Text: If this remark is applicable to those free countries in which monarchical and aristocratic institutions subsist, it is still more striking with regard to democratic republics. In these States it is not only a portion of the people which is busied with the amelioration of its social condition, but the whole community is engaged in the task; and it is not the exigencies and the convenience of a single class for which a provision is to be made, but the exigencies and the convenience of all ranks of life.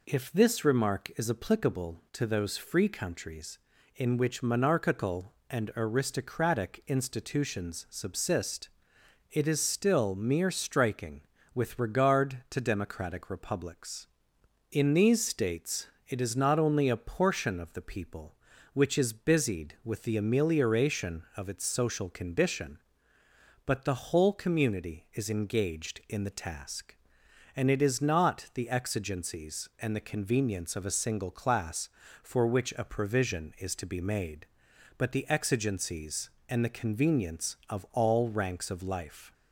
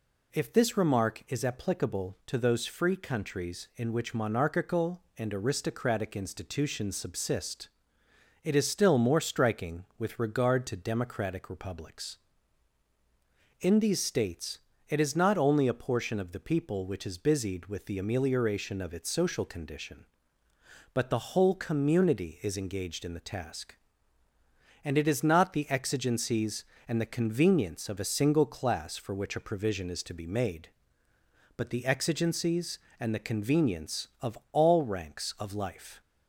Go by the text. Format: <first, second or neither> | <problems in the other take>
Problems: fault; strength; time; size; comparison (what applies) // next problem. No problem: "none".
second | says "mere" for "more"; at 10.1 s // pauses between "States" and "it"; slight; at 15.8 s; 0.22 s long; slight in the second